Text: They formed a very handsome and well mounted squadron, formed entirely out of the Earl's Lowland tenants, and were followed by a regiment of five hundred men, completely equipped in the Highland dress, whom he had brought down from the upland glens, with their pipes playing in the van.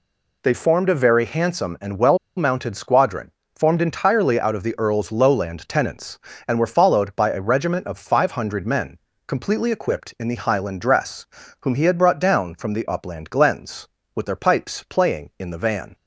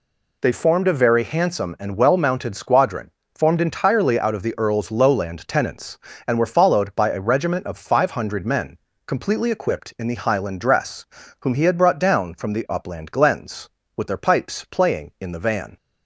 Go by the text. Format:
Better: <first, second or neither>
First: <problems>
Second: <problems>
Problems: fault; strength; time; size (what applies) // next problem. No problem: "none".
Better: second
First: pauses between "well" and "mounted"; slight; at 2.1 s; 0.18 s long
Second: none